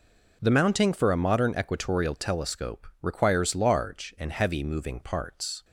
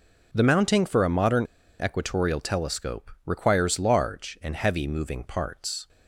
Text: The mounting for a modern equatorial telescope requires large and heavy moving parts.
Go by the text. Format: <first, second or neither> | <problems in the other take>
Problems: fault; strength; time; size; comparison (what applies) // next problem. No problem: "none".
first | pauses between "modern" and "equatorial"; at 1.4 s; 0.39 s long // pauses between "telescope" and "requires"; slight; at 3.1 s; 0.16 s long; slight in the first